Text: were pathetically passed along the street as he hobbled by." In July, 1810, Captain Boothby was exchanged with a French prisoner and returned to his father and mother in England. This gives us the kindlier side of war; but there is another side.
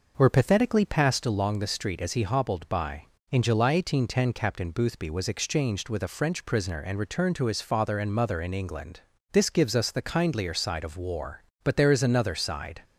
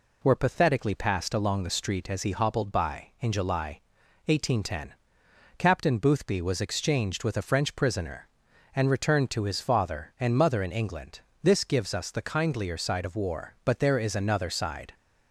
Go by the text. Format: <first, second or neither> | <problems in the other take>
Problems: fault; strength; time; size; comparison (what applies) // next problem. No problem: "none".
second | starts louder than the rest; noticeable; until 1.4 s; 5.5 dB